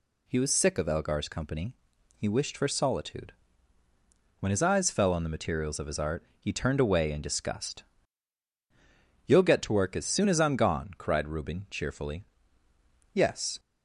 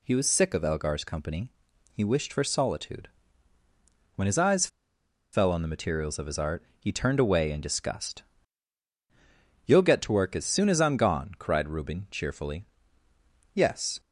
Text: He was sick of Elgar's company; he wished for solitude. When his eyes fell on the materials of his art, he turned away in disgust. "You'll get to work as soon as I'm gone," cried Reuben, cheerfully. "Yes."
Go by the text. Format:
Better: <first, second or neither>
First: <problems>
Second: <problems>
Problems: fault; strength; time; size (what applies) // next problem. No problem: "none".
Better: first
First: none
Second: pauses between "eyes" and "fell"; noticeable; at 4.6 s; 0.65 s long